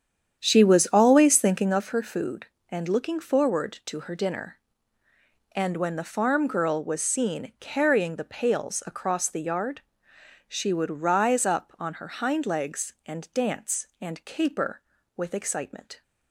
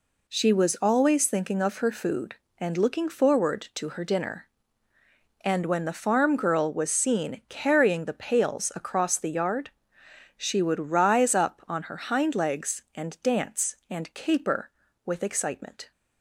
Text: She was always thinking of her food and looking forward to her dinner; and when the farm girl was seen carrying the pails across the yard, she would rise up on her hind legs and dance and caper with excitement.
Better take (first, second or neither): second